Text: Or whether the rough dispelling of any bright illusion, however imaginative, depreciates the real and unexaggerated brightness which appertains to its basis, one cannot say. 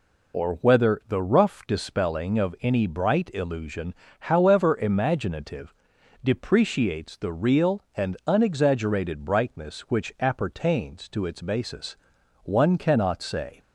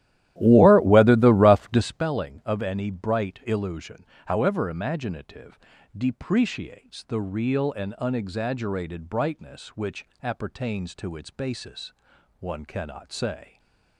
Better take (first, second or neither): first